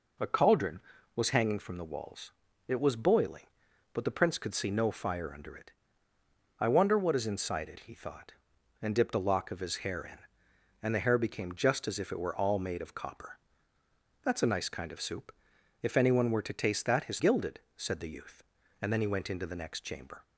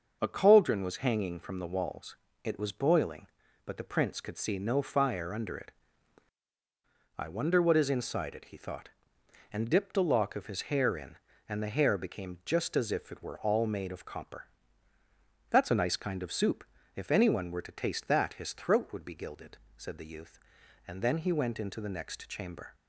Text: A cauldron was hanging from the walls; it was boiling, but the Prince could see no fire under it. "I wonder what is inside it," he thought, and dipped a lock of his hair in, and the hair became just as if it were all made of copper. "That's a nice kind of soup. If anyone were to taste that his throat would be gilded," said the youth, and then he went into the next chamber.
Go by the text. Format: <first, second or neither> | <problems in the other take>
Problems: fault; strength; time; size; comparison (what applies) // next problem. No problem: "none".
second | skips "throat would be"; at 17.1 s